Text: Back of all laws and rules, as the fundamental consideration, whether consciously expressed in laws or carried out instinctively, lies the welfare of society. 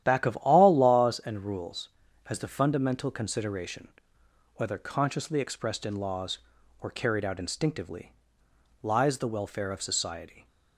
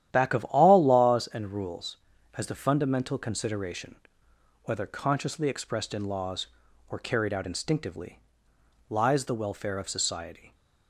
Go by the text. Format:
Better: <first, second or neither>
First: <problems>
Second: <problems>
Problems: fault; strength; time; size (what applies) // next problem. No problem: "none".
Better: neither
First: starts louder than the rest; strong; until 1.0 s; 11 dB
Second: starts louder than the rest; strong; until 1.1 s; 11 dB